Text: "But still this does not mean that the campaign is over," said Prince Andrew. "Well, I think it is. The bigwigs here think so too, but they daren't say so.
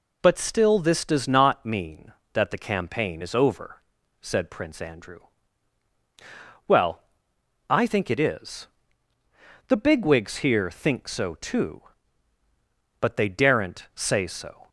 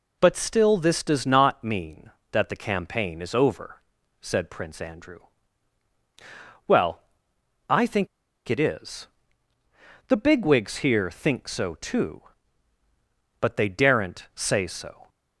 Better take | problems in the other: first | pauses between "think" and "it"; at 8.0 s; 0.41 s long

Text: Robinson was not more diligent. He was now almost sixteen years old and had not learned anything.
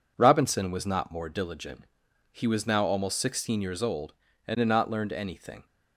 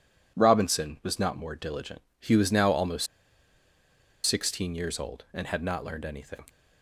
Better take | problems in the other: first | pauses between "almost" and "sixteen"; at 3.0 s; 1.2 s long

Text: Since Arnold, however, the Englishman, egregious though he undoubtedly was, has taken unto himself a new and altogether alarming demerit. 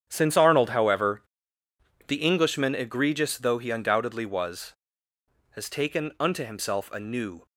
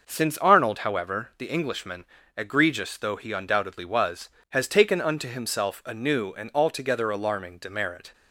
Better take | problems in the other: second | starts louder than the rest; strong; until 1.1 s; 9.5 dB // stops before "and altogether alarming demerit"; at 7.4 s

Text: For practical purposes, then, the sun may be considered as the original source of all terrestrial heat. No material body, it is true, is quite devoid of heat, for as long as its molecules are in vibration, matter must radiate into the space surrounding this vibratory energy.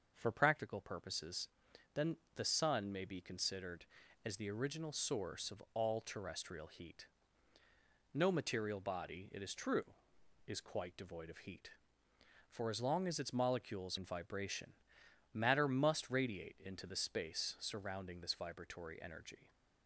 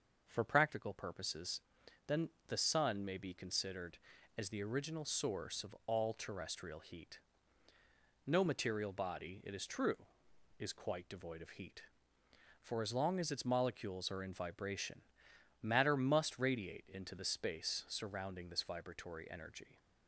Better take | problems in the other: second | starts louder than the rest; noticeable; until 1.1 s; 6 dB; noticeable in the second // skips "are"; at 13.9 s

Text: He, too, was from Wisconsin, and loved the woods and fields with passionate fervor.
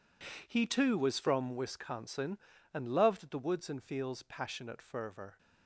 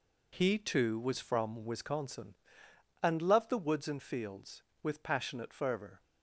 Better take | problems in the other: second | skips "with"; at 4.2 s

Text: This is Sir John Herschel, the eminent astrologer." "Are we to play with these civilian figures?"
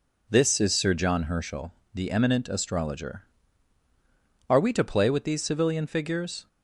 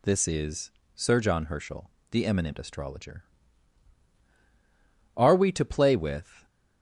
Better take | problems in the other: first | pauses between "is" and "Sir"; slight; at 0.7 s; 0.24 s long // stops before "these civilian figures"; at 6.4 s

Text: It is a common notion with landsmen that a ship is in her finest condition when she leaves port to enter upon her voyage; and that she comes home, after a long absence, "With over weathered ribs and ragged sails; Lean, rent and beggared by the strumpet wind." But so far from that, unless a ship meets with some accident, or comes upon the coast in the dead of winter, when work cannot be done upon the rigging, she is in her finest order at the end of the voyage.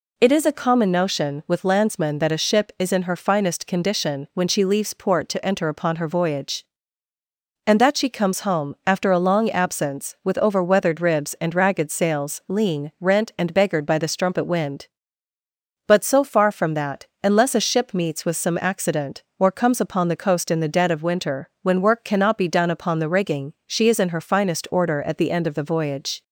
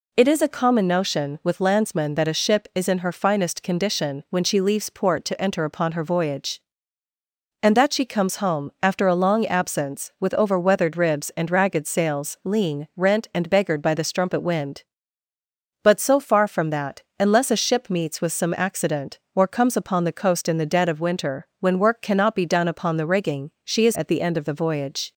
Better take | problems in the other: first | skips "in her finest order"; at 23.9 s

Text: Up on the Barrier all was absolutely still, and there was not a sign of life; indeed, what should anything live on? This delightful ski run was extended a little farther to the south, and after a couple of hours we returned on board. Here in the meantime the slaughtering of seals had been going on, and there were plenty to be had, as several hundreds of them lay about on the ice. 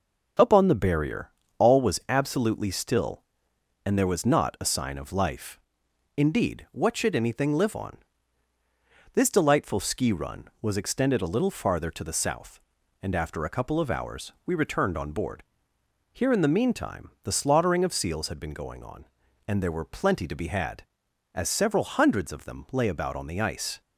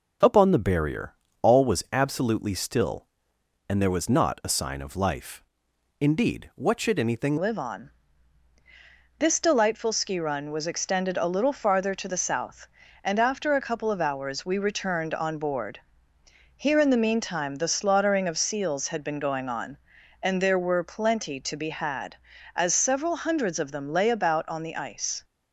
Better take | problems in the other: first | pauses between "Barrier" and "all"; slight; at 1.1 s; 0.26 s long; slight in the first // changes voice at "live"; from 7.3 s on; 17.9 s long

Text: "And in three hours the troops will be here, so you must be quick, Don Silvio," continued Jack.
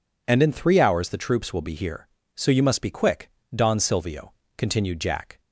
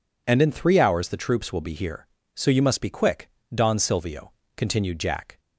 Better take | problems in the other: neither | none

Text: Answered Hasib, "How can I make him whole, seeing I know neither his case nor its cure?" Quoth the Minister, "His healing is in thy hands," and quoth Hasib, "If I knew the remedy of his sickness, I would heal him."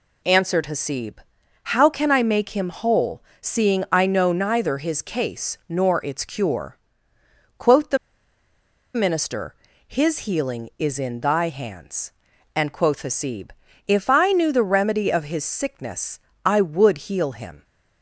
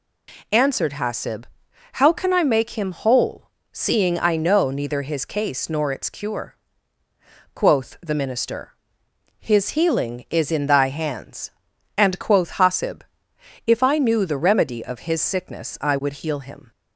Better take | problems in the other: second | pauses between "the" and "Minister"; noticeable; at 7.9 s; 0.98 s long

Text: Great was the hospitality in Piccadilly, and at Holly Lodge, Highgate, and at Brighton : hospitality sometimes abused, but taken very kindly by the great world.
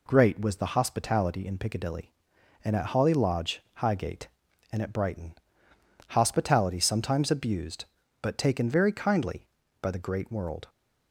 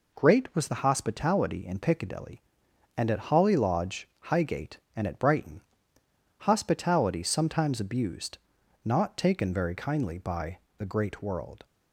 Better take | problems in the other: first | says "not" for "but"; at 8.8 s // pauses between "by" and "the"; slight; at 10.5 s; 0.18 s long

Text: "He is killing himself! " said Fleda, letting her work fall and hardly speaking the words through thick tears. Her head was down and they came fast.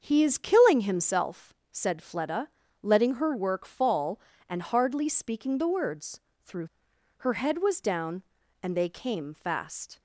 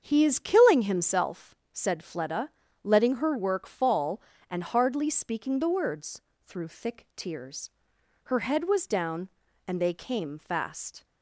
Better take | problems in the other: second | starts louder than the rest; until 1.0 s; 7 dB; strong in the second // pauses between "words" and "through"; slight; at 6.1 s; 0.24 s long; slight in the second // skips "thick tears"; at 6.9 s

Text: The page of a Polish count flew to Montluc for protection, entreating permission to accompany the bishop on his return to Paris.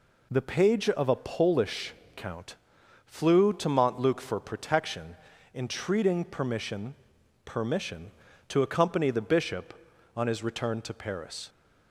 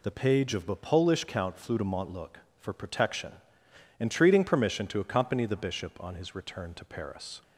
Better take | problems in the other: second | pauses between "Polish" and "count"; slight; at 1.9 s; 0.20 s long // pauses between "count" and "flew"; noticeable; at 2.5 s; 0.52 s long // says "permission" twice; at 7.4 s

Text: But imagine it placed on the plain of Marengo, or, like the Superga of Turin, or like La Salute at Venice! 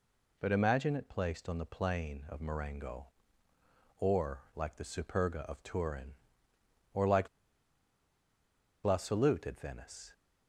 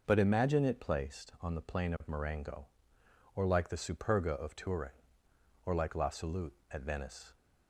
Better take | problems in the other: second | pauses between "like" and "La"; strong; at 7.2 s; 1.5 s long

